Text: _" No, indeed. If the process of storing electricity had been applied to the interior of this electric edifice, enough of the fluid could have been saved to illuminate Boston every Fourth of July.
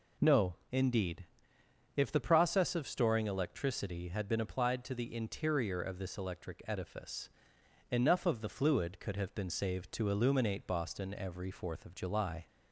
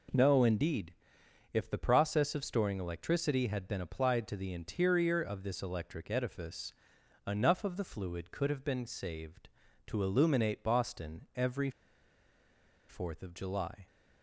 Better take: first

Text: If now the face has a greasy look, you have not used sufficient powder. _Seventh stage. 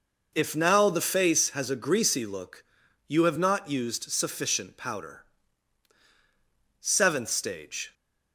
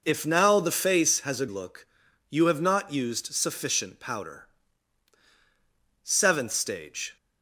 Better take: first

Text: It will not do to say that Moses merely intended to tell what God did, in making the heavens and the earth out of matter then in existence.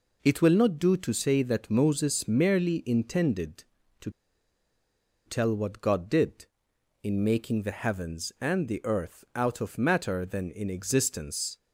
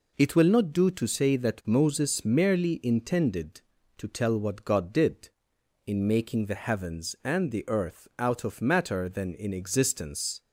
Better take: second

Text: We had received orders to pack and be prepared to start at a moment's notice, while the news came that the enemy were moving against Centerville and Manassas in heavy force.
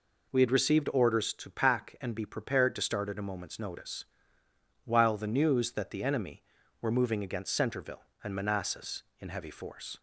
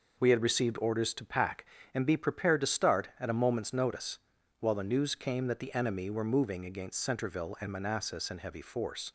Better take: second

